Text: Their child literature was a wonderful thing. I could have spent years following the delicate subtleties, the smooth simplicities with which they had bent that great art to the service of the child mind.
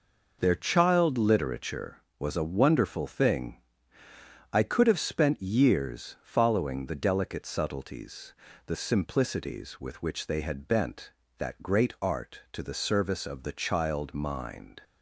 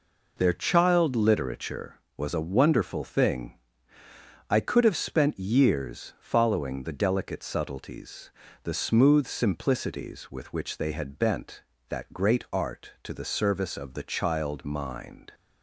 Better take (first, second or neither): second